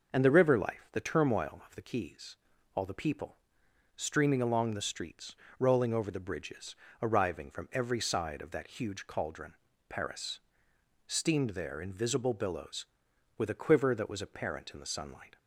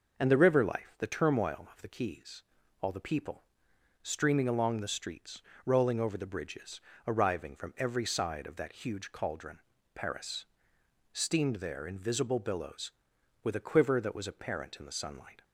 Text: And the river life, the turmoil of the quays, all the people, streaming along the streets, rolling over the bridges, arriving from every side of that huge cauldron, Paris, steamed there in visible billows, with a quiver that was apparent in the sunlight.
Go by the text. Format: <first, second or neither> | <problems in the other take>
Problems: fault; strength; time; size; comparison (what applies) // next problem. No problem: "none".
neither | none